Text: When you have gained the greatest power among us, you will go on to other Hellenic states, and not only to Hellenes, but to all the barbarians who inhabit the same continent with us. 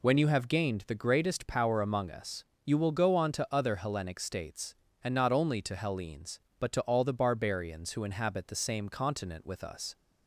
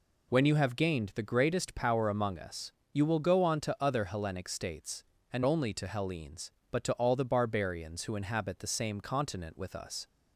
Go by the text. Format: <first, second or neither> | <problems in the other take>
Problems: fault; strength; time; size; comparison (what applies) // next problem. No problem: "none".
first | skips "not"; at 5.4 s